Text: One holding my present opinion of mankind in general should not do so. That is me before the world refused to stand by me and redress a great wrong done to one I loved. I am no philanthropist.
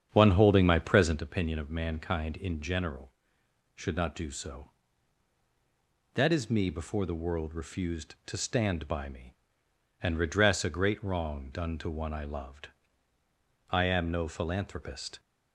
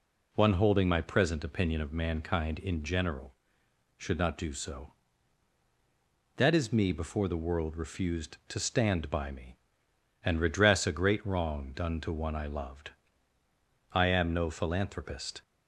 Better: second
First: starts louder than the rest; strong; until 1.2 s; 8 dB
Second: none

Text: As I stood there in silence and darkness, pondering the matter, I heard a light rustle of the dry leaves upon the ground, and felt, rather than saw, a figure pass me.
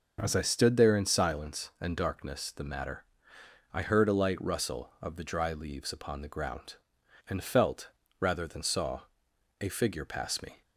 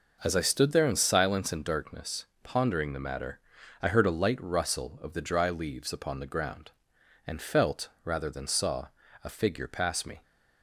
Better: second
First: skips "pondering"; at 2.5 s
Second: none

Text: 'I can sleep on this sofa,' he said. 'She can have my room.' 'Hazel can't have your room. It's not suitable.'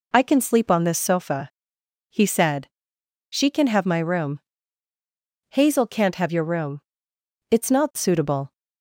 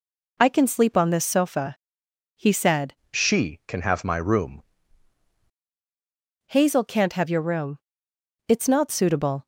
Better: first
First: none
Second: changes voice from "She" to "room"; from 3.1 to 4.6 s; 1.5 s long

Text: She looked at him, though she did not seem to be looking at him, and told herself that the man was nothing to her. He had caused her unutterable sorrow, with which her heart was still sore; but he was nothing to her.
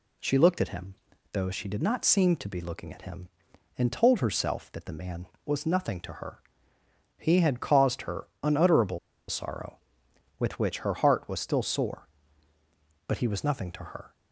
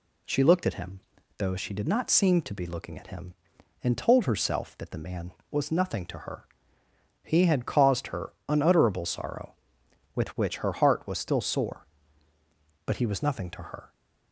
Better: second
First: pauses between "unutterable" and "sorrow"; slight; at 8.9 s; 0.30 s long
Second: none

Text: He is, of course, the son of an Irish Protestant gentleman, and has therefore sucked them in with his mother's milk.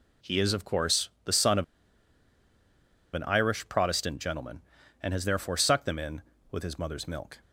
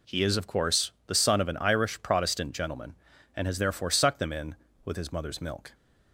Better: second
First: pauses between "of" and "an"; strong; at 1.6 s; 1.5 s long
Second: none

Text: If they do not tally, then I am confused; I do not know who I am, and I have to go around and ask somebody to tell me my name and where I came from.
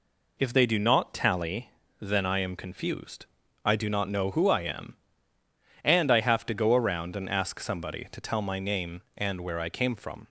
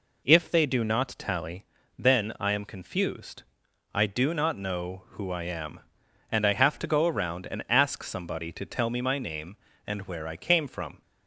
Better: second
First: skips "me"; at 8.4 s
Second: none

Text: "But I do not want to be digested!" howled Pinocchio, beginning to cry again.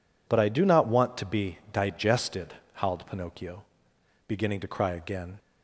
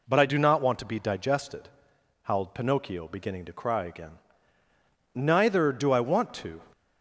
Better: first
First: none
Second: goes on to say "Neither do I want to"; from 5.1 s on; 1.4 s long

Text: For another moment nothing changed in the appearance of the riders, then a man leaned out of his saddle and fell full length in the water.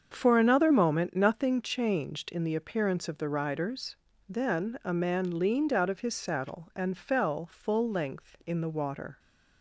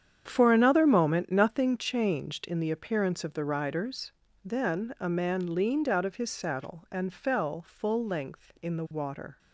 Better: first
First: starts louder than the rest; until 1.1 s; 7 dB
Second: gets quieter; strong; throughout; 12 dB // starts louder than the rest; strong; until 1.2 s; 8.5 dB

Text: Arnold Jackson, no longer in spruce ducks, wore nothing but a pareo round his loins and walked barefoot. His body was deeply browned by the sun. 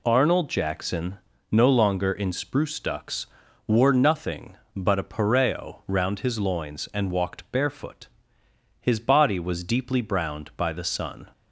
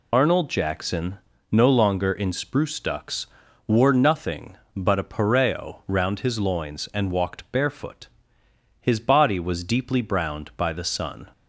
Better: first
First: none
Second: loses the start of "Arnold"; at 0.1 s; 80 ms

